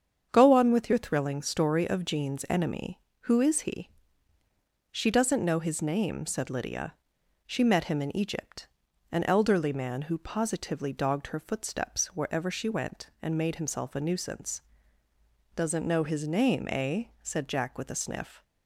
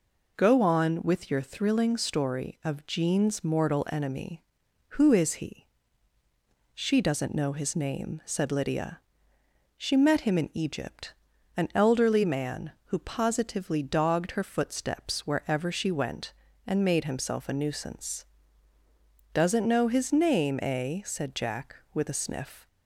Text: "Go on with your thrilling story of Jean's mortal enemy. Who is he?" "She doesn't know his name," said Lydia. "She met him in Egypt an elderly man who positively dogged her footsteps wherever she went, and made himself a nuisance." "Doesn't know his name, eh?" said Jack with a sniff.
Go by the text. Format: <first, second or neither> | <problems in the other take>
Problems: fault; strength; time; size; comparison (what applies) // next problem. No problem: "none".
second | starts louder than the rest; strong; until 1.3 s; 7.5 dB // skips "mortal"; at 2.4 s // pauses between "Egypt" and "an"; at 8.6 s; 0.44 s long; also in the second